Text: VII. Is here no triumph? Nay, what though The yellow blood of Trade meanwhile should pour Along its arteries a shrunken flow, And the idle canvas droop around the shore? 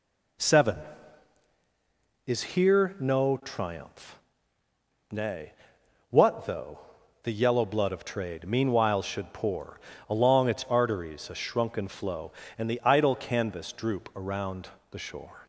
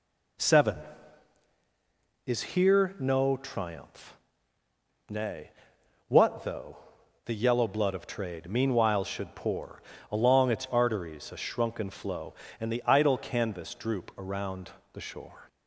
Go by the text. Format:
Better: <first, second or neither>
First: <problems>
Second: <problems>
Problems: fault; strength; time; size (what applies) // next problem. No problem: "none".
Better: neither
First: pauses between "though" and "The"; noticeable; at 6.7 s; 0.46 s long // pauses between "pour" and "Along"; slight; at 9.8 s; 0.26 s long // pauses between "around" and "the"; slight; at 14.6 s; 0.22 s long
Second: pauses between "though" and "The"; noticeable; at 6.7 s; 0.50 s long // pauses between "pour" and "Along"; slight; at 9.8 s; 0.26 s long // pauses between "around" and "the"; slight; at 14.7 s; 0.22 s long